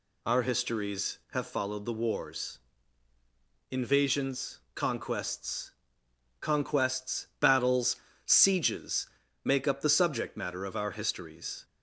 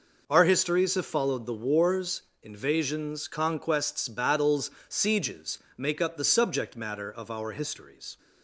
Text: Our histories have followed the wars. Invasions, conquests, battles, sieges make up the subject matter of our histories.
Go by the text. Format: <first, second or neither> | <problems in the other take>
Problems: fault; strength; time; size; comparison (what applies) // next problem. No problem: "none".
second | says "conquests" twice; at 6.4 s // pauses between "sieges" and "make"; at 9.0 s; 0.38 s long; slight in the second